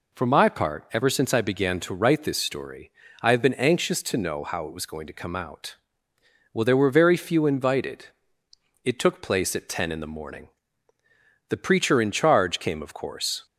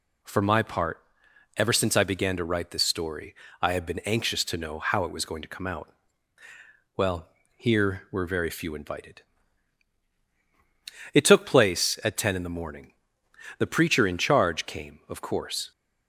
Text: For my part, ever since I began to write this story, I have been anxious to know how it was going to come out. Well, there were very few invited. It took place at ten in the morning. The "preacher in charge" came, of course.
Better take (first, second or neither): first